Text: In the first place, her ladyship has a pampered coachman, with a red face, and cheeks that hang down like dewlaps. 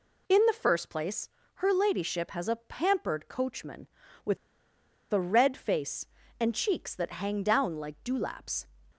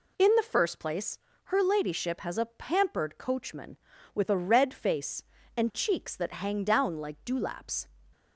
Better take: second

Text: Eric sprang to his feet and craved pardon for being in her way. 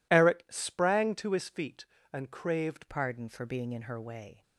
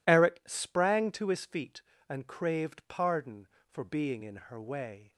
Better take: second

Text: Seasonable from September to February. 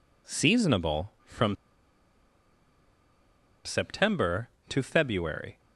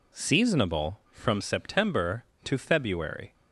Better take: second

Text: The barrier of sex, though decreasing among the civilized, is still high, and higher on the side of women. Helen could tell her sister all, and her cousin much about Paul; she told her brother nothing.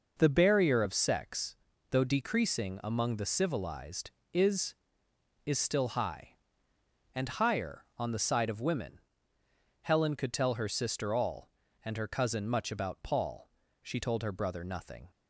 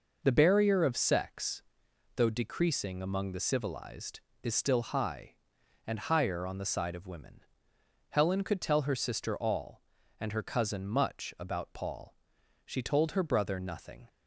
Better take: second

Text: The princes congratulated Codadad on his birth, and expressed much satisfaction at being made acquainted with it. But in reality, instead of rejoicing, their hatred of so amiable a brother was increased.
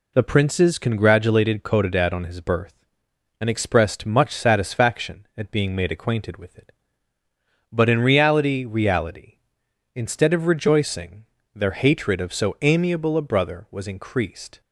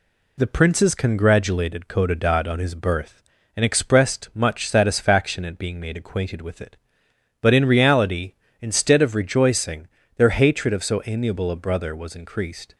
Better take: second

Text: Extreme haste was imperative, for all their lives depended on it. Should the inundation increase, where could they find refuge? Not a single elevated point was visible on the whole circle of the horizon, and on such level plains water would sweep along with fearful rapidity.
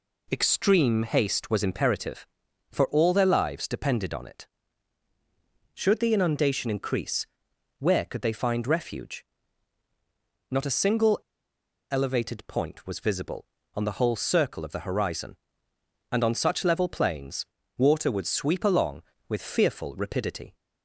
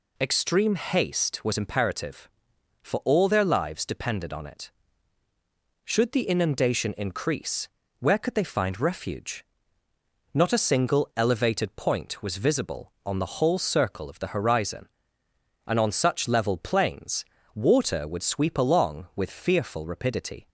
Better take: second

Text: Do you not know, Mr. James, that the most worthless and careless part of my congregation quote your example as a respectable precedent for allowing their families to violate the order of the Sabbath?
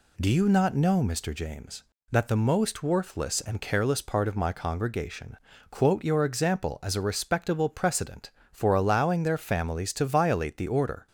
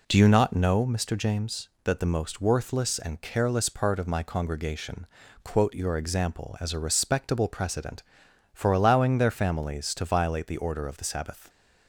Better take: second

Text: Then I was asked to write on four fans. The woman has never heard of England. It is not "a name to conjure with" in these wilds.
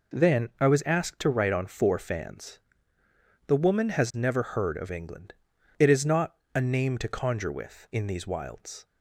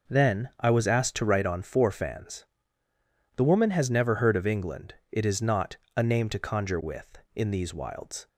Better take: neither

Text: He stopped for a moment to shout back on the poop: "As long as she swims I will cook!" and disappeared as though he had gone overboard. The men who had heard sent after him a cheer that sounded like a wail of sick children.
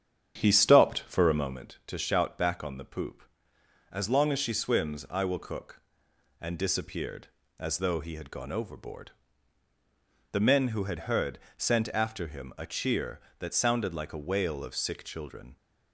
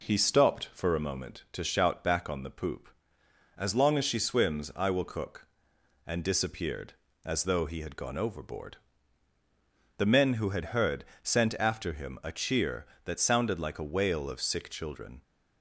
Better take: second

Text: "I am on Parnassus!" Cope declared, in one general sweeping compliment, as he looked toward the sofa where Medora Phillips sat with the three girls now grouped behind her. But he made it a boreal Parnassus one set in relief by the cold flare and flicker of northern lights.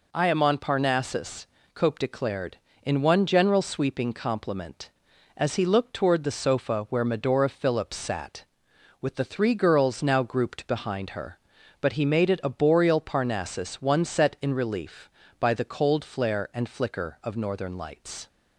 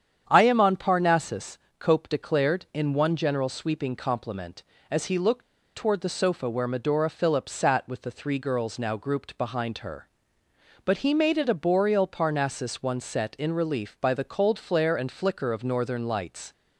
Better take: first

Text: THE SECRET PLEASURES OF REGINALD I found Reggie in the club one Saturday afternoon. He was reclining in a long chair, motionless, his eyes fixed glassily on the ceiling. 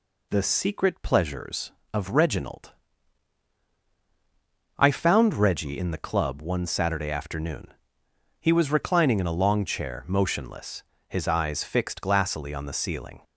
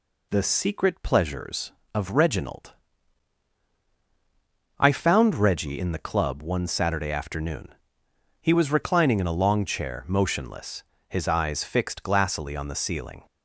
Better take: neither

